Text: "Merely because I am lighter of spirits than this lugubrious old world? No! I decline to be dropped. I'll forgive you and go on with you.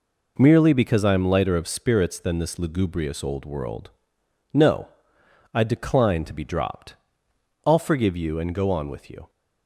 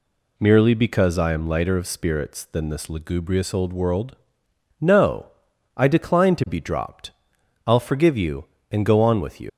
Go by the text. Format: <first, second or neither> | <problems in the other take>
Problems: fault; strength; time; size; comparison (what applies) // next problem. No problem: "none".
first | leaves "you" unfinished; at 9.4 s; 85 ms